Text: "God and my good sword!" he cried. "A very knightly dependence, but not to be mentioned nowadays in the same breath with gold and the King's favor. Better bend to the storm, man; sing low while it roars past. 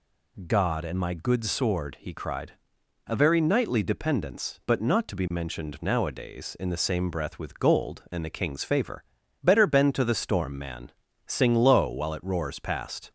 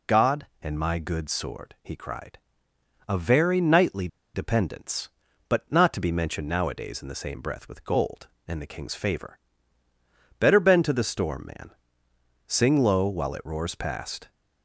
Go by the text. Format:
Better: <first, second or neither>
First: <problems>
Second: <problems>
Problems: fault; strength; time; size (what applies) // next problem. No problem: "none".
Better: first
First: none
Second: pauses between "knightly" and "dependence"; slight; at 4.0 s; 0.26 s long